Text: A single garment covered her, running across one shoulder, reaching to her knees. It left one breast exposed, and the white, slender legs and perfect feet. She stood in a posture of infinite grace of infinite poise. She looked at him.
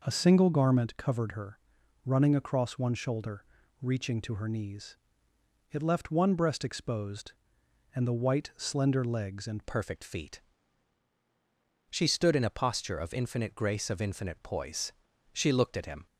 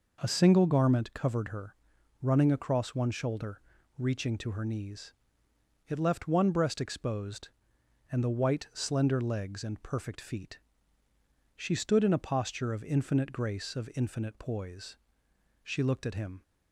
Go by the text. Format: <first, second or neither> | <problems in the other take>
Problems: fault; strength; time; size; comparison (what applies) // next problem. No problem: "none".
second | changes voice at "perfect"; from 9.6 s on; 6.4 s long